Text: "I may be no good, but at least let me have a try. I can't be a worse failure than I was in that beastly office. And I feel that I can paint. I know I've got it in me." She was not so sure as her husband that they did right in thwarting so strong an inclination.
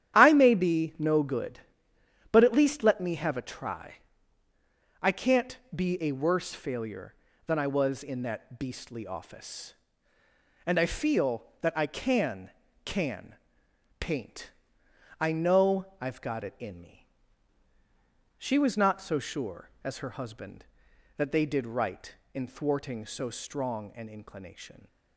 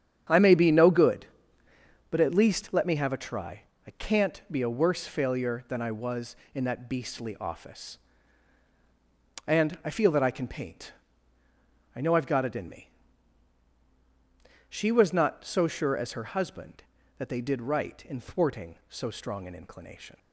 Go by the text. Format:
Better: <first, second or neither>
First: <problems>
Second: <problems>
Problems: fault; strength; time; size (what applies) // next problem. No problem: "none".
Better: second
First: starts louder than the rest; strong; until 1.1 s; 10.5 dB // pauses between "can't" and "be"; slight; at 5.5 s; 0.16 s long // says "can" twice; at 12.8 s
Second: starts louder than the rest; strong; until 2.1 s; 8.5 dB